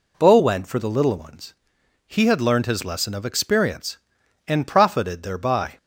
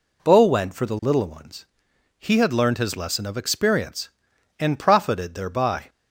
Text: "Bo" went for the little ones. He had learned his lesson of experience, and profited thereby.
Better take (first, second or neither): neither